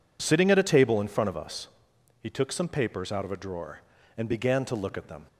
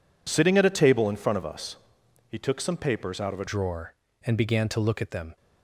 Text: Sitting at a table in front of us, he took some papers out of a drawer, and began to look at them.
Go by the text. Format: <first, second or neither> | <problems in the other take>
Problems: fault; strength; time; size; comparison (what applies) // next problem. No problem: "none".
first | changes voice at "drawer"; from 3.4 s on; 1.9 s long